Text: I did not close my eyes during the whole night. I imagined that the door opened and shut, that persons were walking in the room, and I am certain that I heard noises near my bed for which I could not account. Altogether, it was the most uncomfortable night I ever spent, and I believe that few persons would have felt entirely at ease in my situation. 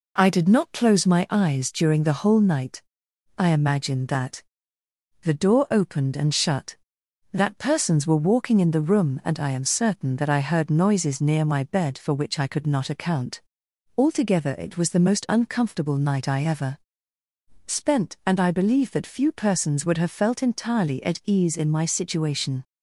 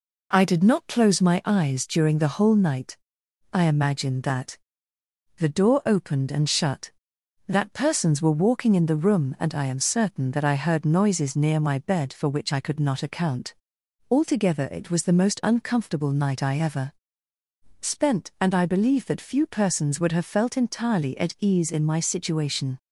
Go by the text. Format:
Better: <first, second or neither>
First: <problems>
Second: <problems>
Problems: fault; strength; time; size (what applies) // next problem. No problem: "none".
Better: neither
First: pauses between "that" and "the"; noticeable; at 4.4 s; 0.80 s long // pauses between "ever" and "spent"; noticeable; at 16.7 s; 0.90 s long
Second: pauses between "that" and "the"; noticeable; at 4.5 s; 0.80 s long // pauses between "ever" and "spent"; noticeable; at 16.9 s; 0.90 s long